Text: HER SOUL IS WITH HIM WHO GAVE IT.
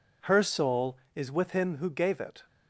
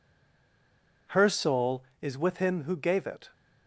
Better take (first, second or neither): first